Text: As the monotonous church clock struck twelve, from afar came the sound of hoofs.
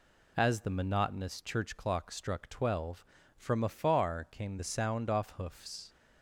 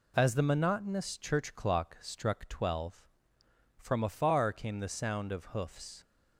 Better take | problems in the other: second | says "off" for "of"; at 5.1 s

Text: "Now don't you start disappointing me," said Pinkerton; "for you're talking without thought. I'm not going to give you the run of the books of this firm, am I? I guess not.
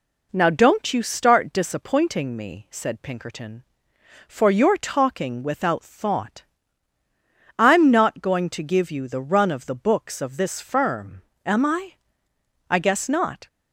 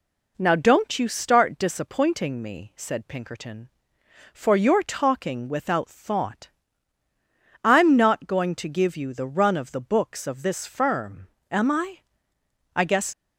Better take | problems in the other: first | stops before "not"; at 13.1 s

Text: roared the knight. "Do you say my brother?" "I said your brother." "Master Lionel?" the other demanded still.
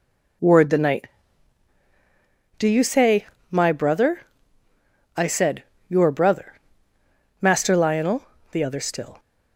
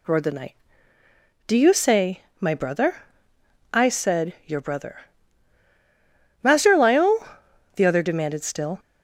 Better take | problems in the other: second | pauses between "say" and "my"; slight; at 3.2 s; 0.26 s long; slight in the second // pauses between "said" and "your"; slight; at 5.6 s; 0.26 s long // skips "demanded"; at 8.7 s

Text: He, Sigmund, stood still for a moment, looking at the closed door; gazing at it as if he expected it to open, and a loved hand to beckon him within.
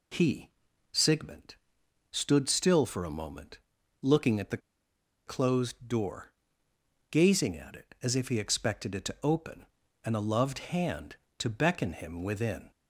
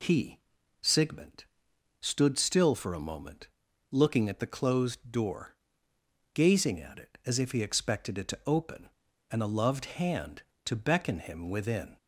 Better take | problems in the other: second | pauses between "the" and "closed"; noticeable; at 4.5 s; 0.68 s long

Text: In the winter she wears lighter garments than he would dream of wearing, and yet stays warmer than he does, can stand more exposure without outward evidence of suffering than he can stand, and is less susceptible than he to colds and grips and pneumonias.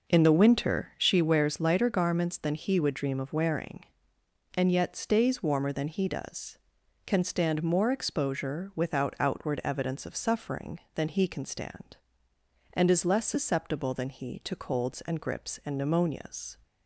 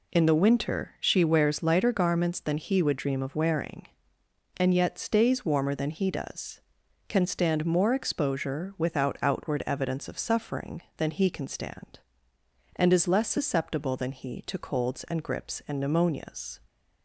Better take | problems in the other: second | starts louder than the rest; noticeable; until 1.2 s; 5.5 dB

